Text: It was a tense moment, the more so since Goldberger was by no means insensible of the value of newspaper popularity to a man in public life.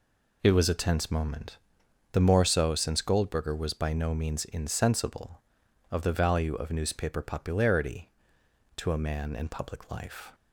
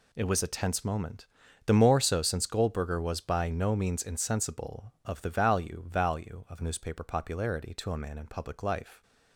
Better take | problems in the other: first | says "value" twice; at 5.8 s

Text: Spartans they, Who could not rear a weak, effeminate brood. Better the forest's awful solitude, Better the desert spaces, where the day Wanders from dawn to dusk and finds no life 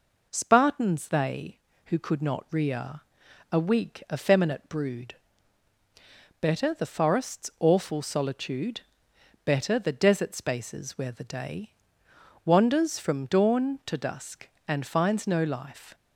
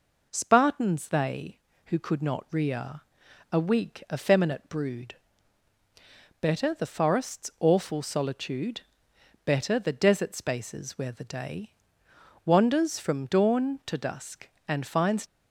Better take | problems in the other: first | pauses between "rear" and "a"; noticeable; at 3.0 s; 0.50 s long; noticeable in the first // pauses between "day" and "Wanders"; noticeable; at 11.7 s; 0.74 s long; noticeable in the first // stops before "no life"; at 15.2 s

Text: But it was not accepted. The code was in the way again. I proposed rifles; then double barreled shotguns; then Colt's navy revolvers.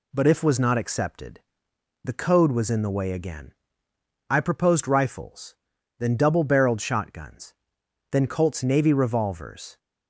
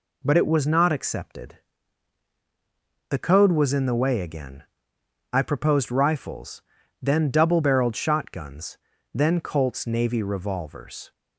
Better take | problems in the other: second | says "if" for "it"; at 0.2 s

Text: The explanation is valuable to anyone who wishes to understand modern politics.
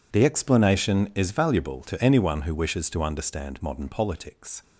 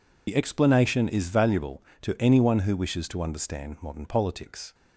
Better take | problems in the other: first | loses the start of "The"; at 0.2 s; 55 ms

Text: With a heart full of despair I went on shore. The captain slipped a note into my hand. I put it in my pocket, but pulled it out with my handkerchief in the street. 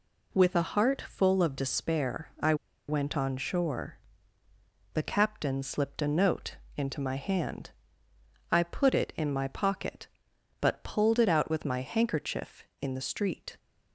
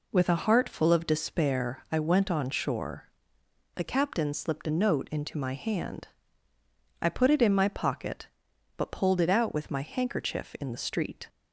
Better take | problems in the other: second | pauses between "I" and "went"; slight; at 2.5 s; 0.34 s long // pauses between "note" and "into"; slight; at 6.5 s; 0.20 s long

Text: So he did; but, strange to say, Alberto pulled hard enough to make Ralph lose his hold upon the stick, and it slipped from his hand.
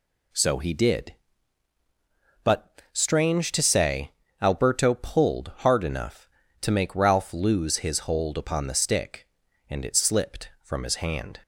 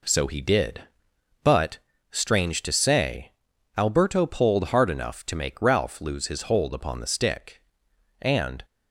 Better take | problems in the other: first | stops before "it slipped from his hand"; at 8.6 s

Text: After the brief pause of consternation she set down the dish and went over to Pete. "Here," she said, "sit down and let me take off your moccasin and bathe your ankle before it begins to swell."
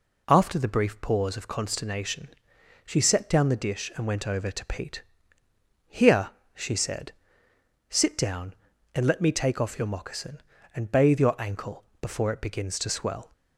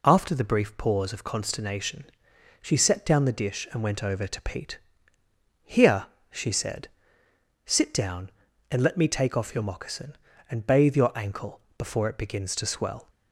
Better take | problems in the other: neither | pauses between "consternation" and "she"; noticeable; the same in both // pauses between "ankle" and "before"; slight; the same in both

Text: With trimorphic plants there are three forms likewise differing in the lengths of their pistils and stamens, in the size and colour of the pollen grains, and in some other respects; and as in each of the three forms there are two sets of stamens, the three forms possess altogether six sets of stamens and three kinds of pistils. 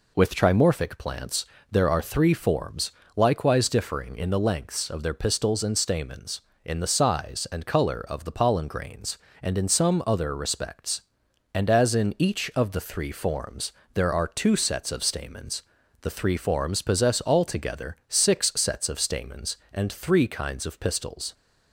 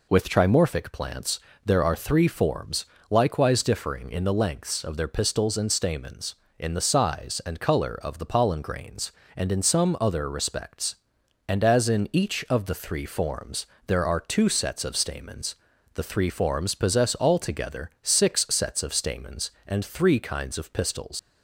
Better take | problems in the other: first | pauses between "plants" and "there"; slight; at 1.3 s; 0.24 s long; slight in the first // pauses between "forms" and "likewise"; slight; at 2.8 s; 0.24 s long; slight in the first // pauses between "forms" and "there"; slight; at 13.6 s; 0.20 s long; slight in the first // leaves "pistils" unfinished; at 21.1 s; 70 ms

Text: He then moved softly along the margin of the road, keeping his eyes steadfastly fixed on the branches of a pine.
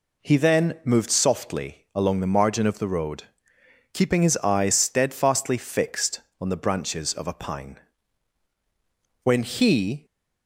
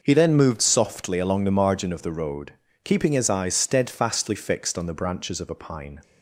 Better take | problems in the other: second | goes on to say "When he"; noticeable; from 9.2 s on; 0.82 s long

